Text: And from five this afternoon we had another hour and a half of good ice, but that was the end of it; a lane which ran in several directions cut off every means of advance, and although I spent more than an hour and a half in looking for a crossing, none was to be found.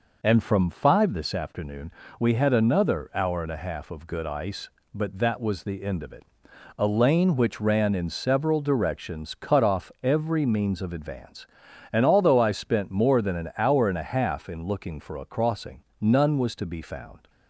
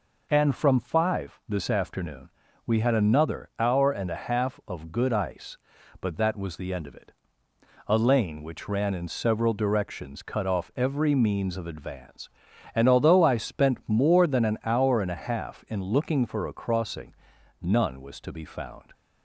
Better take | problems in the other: neither | pauses between "afternoon" and "we"; slight; the same in both

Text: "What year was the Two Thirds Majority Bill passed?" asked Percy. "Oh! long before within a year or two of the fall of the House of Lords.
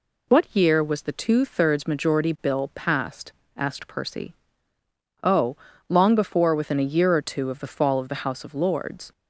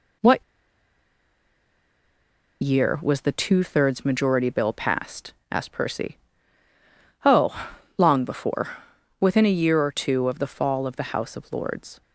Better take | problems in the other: first | pauses between "What" and "year"; strong; at 0.4 s; 2.1 s long // pauses between "before" and "within"; noticeable; at 8.6 s; 0.54 s long

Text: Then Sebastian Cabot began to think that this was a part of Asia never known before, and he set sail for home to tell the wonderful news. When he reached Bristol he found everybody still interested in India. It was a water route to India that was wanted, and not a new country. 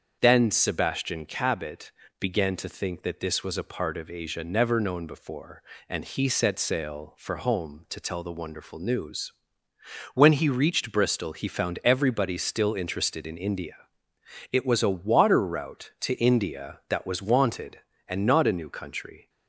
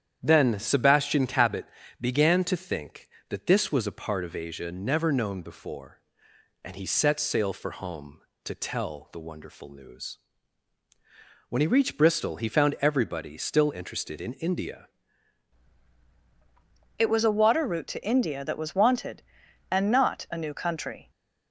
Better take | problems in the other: first | starts louder than the rest; strong; until 1.2 s; 9 dB; also in the first // pauses between "Cabot" and "began"; slight; at 1.6 s; 0.36 s long; slight in the first // changes voice at "It"; from 16.9 s on; 4.1 s long

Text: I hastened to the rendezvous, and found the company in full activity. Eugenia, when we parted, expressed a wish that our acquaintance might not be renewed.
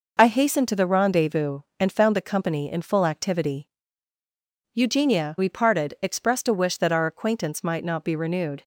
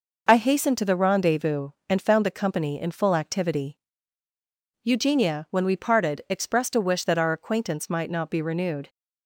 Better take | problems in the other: second | skips "when"; at 5.3 s

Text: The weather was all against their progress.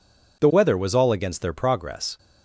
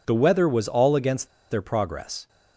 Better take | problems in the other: first | pauses between "against" and "their"; slight; at 1.2 s; 0.23 s long

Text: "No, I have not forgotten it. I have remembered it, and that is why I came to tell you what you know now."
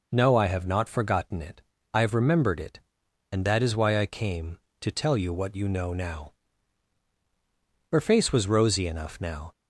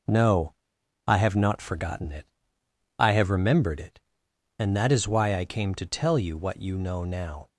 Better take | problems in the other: second | goes on to say "Her face was rosy enough now"; from 7.9 s on; 1.6 s long

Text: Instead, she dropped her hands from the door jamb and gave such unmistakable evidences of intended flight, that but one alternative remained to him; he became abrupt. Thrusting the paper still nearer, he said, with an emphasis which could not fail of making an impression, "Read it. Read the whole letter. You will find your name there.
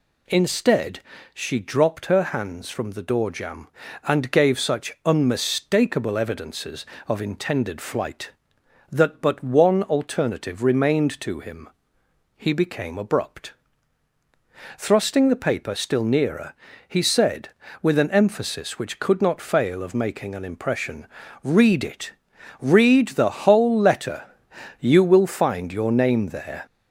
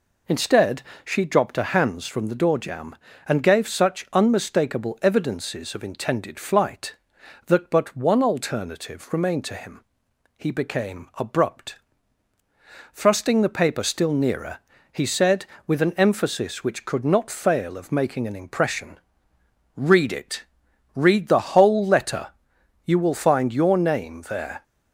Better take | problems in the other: neither | none

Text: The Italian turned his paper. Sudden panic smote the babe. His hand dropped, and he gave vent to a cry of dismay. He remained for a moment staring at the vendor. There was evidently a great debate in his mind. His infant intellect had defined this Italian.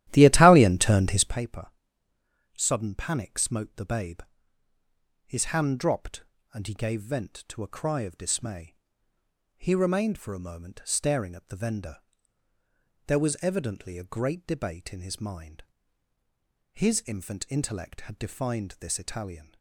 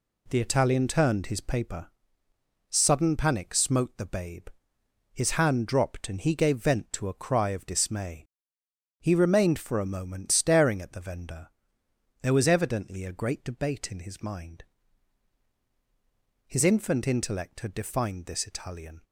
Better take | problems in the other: second | starts louder than the rest; strong; until 1.4 s; 13.5 dB

